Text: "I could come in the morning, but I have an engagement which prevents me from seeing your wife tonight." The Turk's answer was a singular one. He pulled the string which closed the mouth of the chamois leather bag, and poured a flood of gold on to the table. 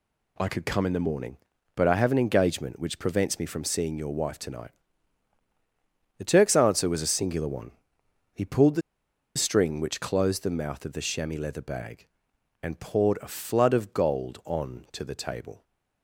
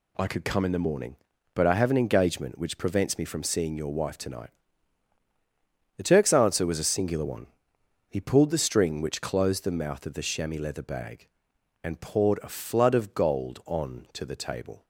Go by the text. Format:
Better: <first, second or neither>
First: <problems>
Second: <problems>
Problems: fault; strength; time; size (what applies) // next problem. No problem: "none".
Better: second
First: pauses between "the" and "string"; noticeable; at 8.8 s; 0.56 s long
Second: none